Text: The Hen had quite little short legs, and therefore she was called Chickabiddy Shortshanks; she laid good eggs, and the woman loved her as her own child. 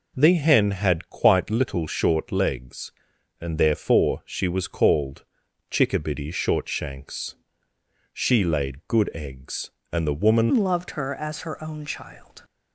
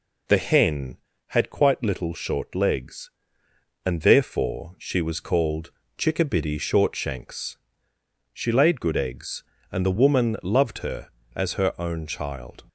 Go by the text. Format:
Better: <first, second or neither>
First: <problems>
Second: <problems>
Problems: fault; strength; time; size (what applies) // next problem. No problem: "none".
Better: second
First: pauses between "called" and "Chickabiddy"; noticeable; at 5.2 s; 0.46 s long // changes voice at "loved"; from 10.5 s on; 1.8 s long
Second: pauses between "called" and "Chickabiddy"; slight; at 5.7 s; 0.28 s long